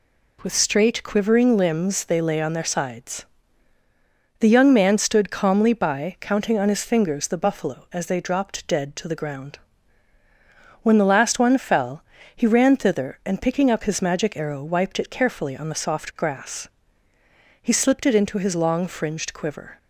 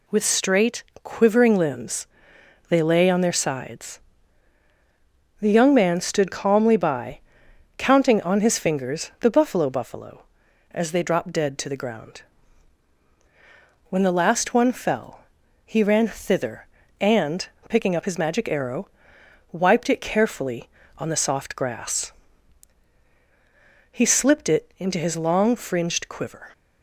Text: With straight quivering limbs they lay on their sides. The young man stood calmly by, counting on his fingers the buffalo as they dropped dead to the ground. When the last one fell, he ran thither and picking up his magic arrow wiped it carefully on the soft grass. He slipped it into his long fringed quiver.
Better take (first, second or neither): first